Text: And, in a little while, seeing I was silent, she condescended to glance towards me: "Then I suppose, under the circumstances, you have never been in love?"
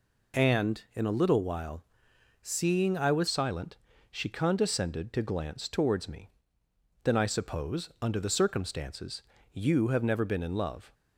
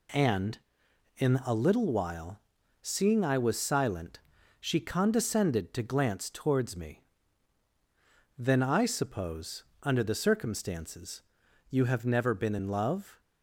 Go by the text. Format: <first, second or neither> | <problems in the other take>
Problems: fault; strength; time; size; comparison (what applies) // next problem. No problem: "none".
second | changes voice at "silent"; from 3.2 s on; 7.7 s long